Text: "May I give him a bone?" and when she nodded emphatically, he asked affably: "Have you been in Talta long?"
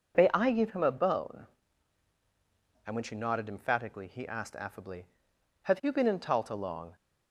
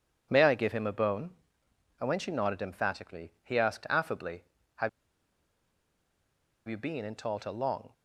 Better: first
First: none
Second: pauses between "Have" and "you"; strong; at 4.8 s; 1.7 s long

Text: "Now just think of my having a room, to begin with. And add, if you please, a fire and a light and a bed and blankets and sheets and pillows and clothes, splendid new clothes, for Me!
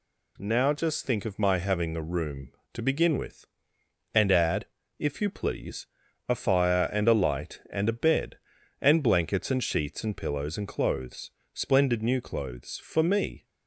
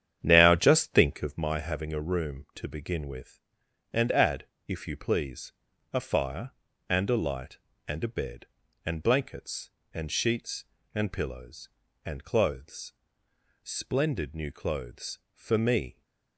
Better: first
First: none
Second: starts louder than the rest; strong; until 1.4 s; 9.5 dB

